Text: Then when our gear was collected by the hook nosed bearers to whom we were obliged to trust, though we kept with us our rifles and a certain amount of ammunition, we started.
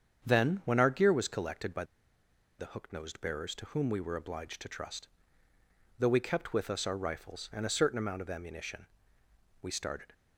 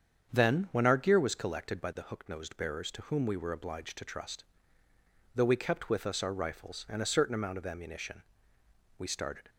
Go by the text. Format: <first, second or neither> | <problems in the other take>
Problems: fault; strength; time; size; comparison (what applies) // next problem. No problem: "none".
second | starts louder than the rest; strong; until 1.3 s; 7.5 dB; strong in the second // pauses between "by" and "the"; noticeable; at 1.8 s; 0.74 s long